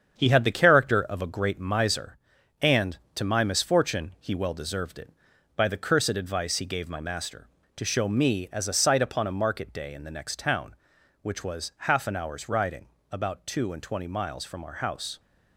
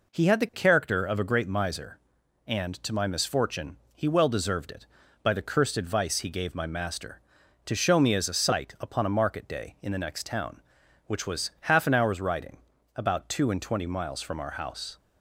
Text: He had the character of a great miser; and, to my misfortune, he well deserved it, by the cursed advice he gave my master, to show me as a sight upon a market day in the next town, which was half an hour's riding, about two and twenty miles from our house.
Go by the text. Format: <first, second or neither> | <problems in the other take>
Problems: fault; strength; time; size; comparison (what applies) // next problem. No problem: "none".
second | gets quieter; throughout; 6.5 dB